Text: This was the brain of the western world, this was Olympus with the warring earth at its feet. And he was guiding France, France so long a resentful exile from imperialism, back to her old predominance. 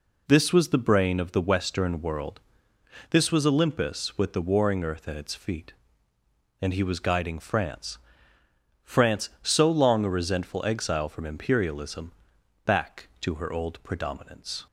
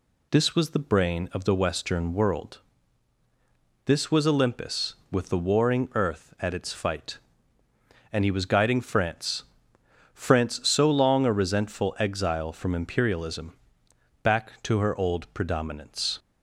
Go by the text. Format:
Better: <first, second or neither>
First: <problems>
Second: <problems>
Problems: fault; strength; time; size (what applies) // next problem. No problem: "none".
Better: first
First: none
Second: says "fight" for "feet"; at 6.7 s